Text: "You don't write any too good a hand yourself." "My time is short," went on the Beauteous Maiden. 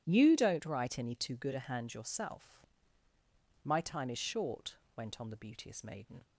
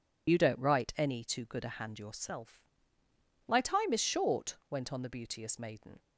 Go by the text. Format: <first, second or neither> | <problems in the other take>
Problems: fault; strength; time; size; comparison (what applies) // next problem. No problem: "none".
first | loses the start of "You"; at 0.2 s; 50 ms